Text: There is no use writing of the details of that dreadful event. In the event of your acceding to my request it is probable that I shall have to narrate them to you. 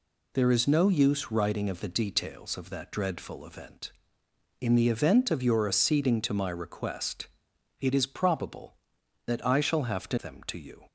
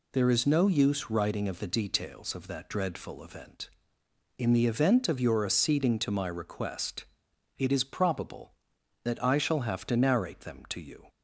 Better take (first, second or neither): second